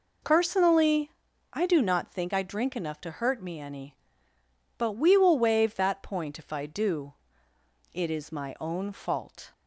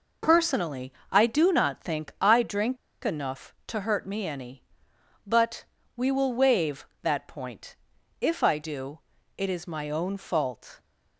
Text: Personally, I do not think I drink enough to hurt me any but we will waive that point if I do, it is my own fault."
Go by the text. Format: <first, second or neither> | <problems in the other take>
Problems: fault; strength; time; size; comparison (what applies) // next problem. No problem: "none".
first | pauses between "drink" and "enough"; slight; at 2.7 s; 0.28 s long // pauses between "but" and "we"; slight; at 5.6 s; 0.32 s long // pauses between "point" and "if"; at 7.7 s; 0.44 s long